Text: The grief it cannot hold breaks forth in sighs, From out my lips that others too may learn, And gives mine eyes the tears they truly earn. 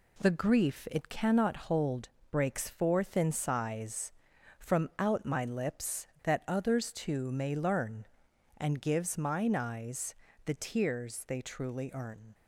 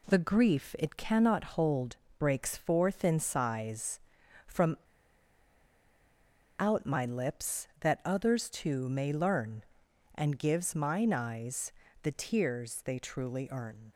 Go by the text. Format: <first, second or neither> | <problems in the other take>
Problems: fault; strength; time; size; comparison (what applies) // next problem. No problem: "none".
first | pauses between "hold" and "breaks"; slight; at 1.9 s; 0.22 s long; slight in the first // pauses between "From" and "out"; strong; at 4.7 s; 1.8 s long // pauses between "eyes" and "the"; slight; at 11.7 s; 0.30 s long; slight in the first